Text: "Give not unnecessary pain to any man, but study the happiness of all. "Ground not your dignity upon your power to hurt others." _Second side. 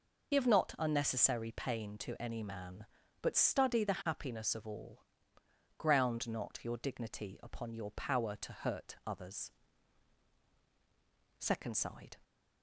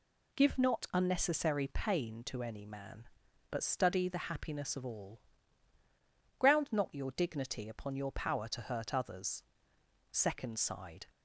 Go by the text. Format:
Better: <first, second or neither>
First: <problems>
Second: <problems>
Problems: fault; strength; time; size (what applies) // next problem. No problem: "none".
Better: second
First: loses the start of "Give"; at 0.3 s; 45 ms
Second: none